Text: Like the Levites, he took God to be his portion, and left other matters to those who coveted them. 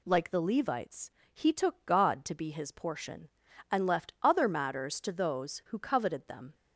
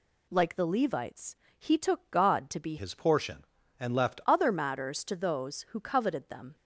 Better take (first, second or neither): first